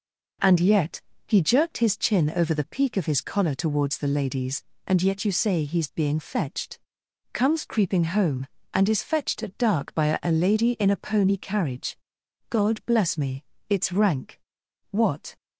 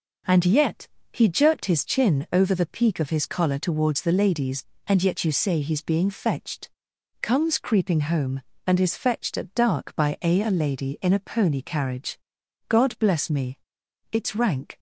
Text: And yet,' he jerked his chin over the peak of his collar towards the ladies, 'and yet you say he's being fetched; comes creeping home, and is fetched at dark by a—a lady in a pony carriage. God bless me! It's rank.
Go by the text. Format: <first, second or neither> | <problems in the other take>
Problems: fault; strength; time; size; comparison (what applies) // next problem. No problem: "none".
second | goes on to say "What"; slight; from 14.9 s on; 0.44 s long